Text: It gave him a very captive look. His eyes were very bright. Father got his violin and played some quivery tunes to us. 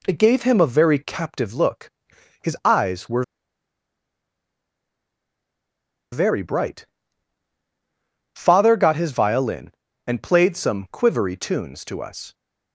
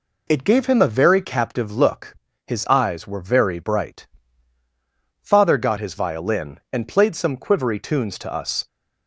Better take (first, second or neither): second